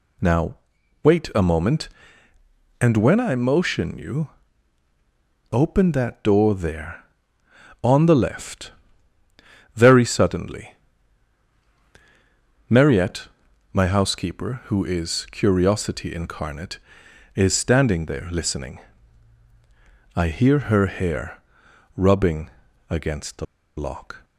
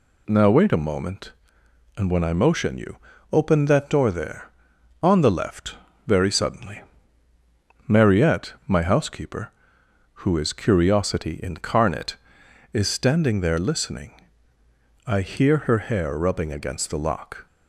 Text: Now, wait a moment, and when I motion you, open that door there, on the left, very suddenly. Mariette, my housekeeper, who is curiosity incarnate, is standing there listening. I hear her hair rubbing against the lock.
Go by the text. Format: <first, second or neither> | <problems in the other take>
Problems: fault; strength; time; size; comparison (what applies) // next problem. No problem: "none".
second | pauses between "hair" and "rubbing"; noticeable; at 21.4 s; 0.56 s long // pauses between "rubbing" and "against"; at 22.5 s; 0.40 s long // pauses between "the" and "lock"; slight; at 23.4 s; 0.32 s long